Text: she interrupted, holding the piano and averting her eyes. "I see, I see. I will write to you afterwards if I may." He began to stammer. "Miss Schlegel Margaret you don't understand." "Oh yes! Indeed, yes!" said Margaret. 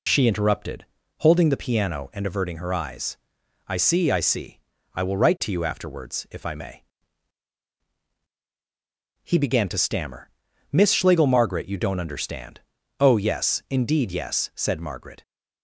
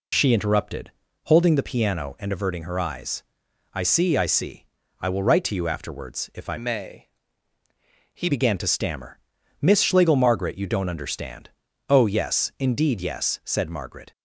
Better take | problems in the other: first | changes voice from "may" to "He"; from 6.5 to 8.2 s; 1.7 s long

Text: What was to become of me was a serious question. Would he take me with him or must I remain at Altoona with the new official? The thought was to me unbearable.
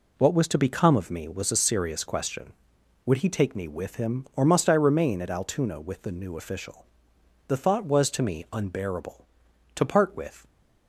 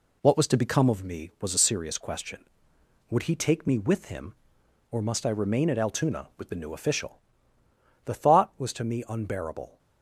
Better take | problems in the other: second | goes on to say "To part with"; noticeable; from 9.7 s on; 0.72 s long

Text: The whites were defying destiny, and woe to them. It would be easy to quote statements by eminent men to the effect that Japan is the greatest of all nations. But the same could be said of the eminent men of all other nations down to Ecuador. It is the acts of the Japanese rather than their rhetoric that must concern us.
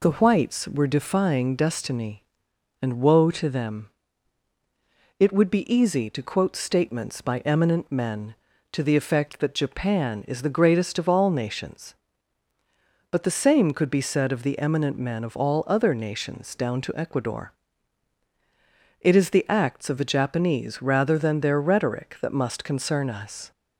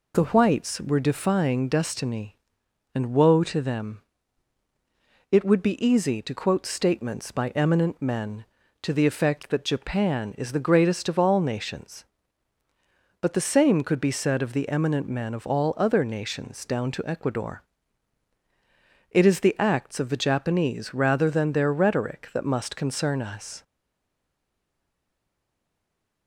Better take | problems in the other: first | stays silent after the last word; strong; from 23.6 s on; 2.6 s long

